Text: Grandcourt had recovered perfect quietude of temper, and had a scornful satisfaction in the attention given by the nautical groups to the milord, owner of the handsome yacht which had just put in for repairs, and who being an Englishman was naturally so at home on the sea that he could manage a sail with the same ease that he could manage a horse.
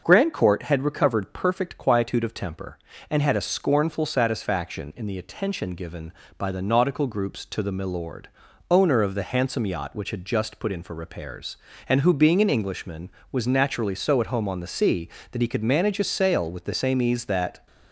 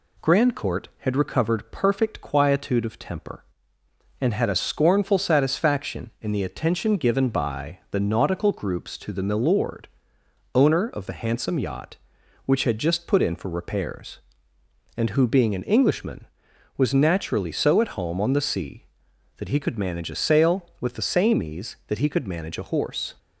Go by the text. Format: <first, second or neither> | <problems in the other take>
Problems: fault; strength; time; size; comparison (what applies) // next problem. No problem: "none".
second | stops before "he could manage a horse"; at 17.6 s